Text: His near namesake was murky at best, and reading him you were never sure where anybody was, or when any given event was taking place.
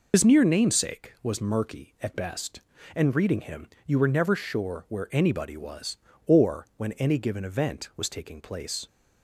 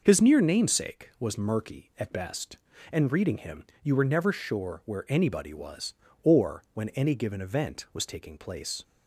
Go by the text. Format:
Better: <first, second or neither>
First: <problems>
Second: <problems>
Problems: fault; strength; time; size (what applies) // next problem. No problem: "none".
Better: second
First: loses the start of "His"; at 0.1 s; 60 ms // pauses between "him" and "you"; slight; at 3.6 s; 0.20 s long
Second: pauses between "him" and "you"; slight; at 3.6 s; 0.20 s long